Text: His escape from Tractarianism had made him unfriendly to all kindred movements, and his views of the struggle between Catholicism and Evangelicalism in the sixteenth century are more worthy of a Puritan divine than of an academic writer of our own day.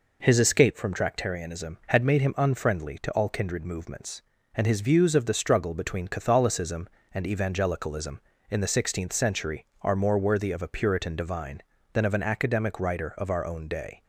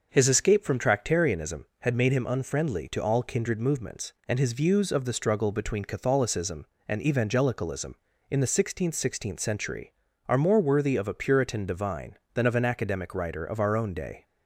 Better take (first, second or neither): first